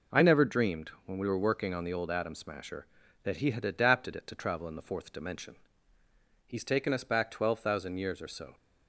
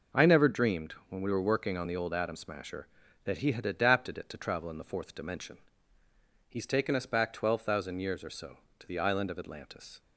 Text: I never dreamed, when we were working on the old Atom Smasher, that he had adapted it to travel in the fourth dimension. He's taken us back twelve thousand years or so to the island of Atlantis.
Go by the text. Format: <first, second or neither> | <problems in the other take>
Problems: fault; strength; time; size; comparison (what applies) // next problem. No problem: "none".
second | stops before "to the island of Atlantis"; at 8.5 s